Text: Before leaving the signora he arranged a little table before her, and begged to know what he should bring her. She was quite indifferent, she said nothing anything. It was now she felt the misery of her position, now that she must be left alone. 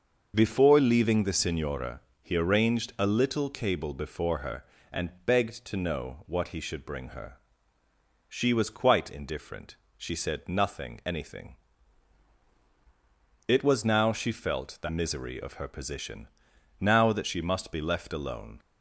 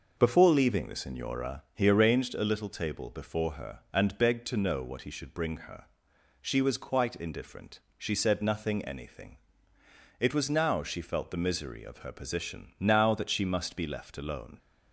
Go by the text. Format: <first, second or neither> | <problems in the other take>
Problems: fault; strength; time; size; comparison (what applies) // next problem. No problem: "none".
second | starts louder than the rest; noticeable; until 1.3 s; 6 dB // pauses between "signora" and "he"; slight; at 2.0 s; 0.20 s long // says "cable" for "table"; at 3.4 s